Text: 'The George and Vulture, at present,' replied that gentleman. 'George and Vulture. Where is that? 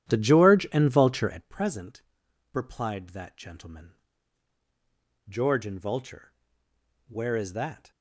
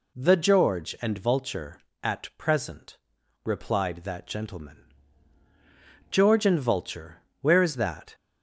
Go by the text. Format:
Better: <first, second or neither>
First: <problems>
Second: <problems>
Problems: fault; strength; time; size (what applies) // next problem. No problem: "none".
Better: second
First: starts louder than the rest; strong; until 1.6 s; 11 dB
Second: none